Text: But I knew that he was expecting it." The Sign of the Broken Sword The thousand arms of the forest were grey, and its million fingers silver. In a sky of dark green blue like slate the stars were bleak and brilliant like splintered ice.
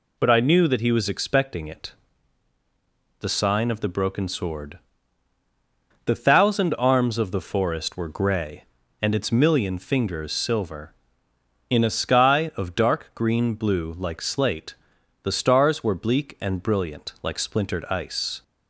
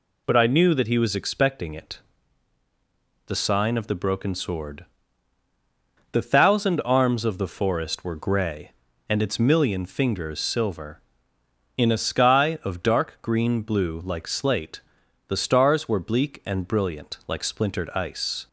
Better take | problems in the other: neither | pauses between "Sword" and "The"; strong; the same in both // pauses between "slate" and "the"; noticeable; the same in both

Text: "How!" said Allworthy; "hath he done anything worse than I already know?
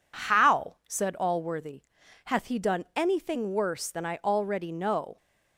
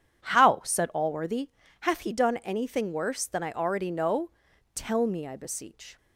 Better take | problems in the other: first | goes on to say "Tell me I beseech"; noticeable; from 4.7 s on; 1.2 s long

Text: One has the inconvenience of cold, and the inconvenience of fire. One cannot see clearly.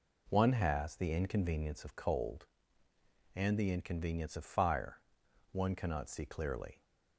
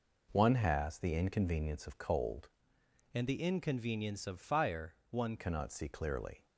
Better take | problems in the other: first | changes voice from "and" to "One"; from 3.1 to 5.3 s; 2.2 s long

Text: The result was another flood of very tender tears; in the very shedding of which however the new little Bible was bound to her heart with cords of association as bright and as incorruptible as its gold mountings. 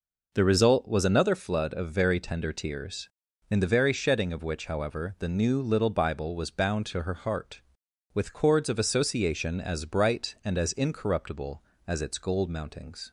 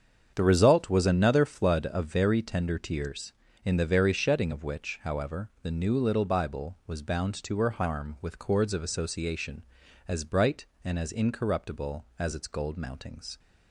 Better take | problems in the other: first | starts louder than the rest; strong; until 1.3 s; 7.5 dB // says "harm" for "heart"; at 7.7 s

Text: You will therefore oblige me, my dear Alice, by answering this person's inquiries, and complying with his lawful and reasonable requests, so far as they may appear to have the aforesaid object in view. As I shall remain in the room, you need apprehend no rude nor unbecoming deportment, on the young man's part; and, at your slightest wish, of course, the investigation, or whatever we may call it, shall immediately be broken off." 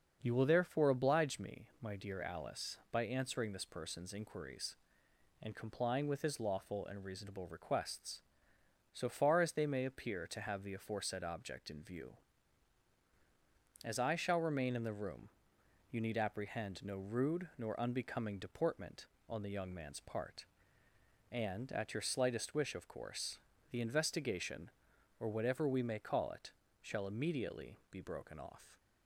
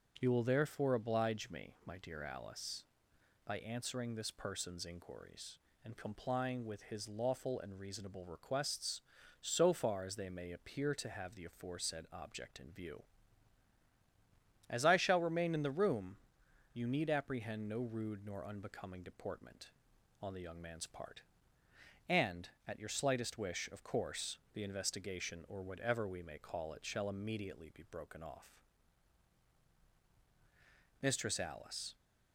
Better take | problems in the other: first | starts louder than the rest; noticeable; until 1.1 s; 6 dB; also in the first // goes on to say "Mistress Alice"; noticeable; from 31.0 s on; 0.92 s long

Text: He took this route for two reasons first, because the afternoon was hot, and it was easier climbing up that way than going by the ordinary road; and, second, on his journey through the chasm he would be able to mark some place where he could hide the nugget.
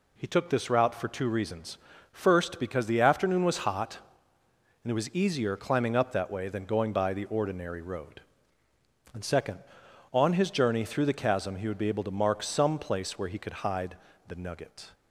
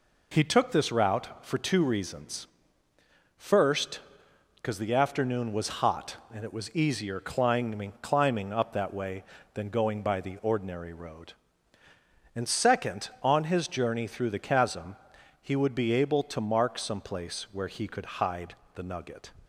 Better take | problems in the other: first | pauses between "reasons" and "first"; noticeable; at 2.4 s; 0.90 s long; slight in the first // says "climbing" twice; at 8.0 s // pauses between "chasm" and "he"; noticeable; at 14.9 s; 0.46 s long // pauses between "hide" and "the"; slight; at 18.5 s; 0.20 s long; slight in the first

